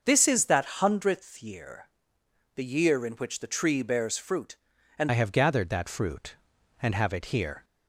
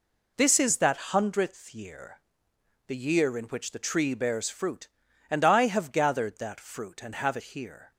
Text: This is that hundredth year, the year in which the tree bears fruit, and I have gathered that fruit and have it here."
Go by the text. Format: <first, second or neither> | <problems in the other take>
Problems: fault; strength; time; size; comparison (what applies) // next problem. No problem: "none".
second | starts louder than the rest; until 1.0 s; 6 dB // changes voice at "I"; from 5.0 s on; 2.6 s long